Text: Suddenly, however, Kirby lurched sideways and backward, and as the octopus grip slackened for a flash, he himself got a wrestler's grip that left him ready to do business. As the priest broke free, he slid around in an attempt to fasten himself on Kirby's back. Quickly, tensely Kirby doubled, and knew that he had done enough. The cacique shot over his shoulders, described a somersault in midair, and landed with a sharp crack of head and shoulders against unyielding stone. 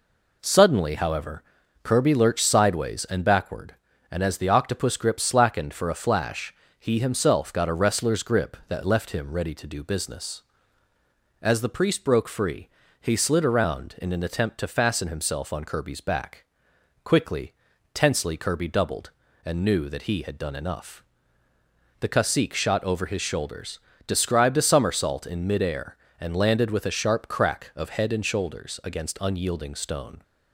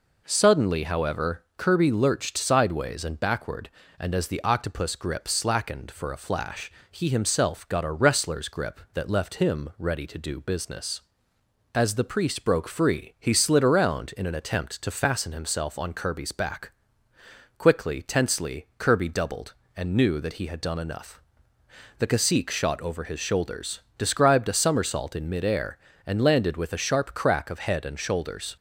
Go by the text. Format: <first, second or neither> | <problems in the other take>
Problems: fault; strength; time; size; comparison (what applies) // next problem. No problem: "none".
first | stops before "against unyielding stone"; at 28.5 s